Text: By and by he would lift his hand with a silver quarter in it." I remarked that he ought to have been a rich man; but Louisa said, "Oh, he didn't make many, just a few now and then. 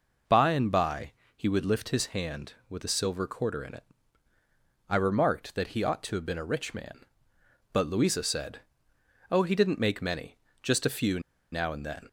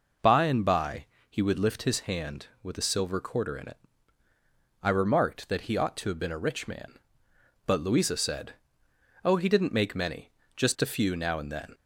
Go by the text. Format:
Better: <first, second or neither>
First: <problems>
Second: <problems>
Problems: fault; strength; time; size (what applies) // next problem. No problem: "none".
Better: second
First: pauses between "by" and "he"; slight; at 1.1 s; 0.24 s long // pauses between "few" and "now"; slight; at 11.1 s; 0.32 s long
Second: pauses between "by" and "he"; slight; at 1.0 s; 0.24 s long